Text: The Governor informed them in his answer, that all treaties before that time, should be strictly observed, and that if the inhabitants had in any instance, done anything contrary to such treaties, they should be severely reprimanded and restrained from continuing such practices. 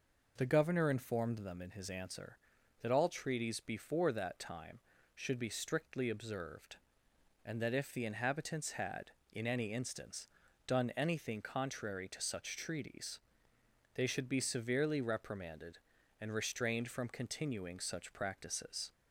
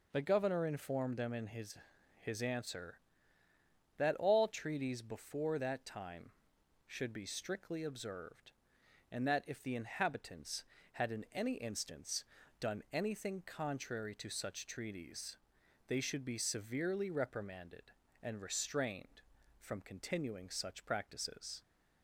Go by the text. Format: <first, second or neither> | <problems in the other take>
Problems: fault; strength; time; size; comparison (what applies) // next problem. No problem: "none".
first | says "his" twice; at 2.1 s